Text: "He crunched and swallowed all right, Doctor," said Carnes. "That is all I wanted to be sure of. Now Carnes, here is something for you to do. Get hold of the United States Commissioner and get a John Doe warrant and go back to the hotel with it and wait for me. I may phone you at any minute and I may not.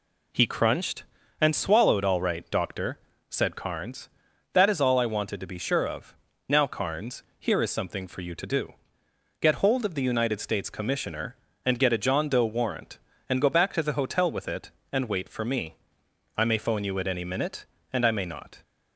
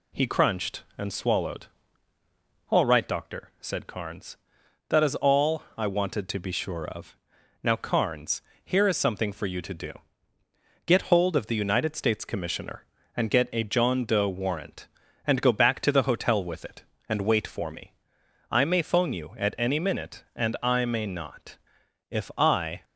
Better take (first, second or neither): first